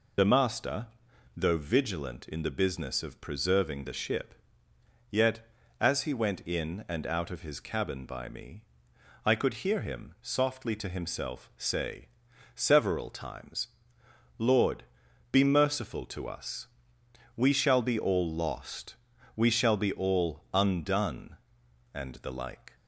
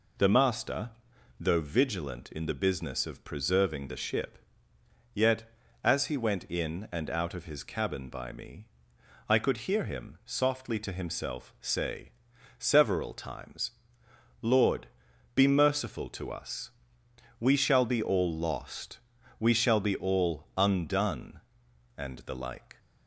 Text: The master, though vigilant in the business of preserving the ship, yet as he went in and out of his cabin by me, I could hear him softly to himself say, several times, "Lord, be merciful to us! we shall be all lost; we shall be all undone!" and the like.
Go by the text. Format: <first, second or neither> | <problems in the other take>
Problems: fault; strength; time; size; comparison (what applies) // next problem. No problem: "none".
second | loses the start of "The"; at 0.1 s; 35 ms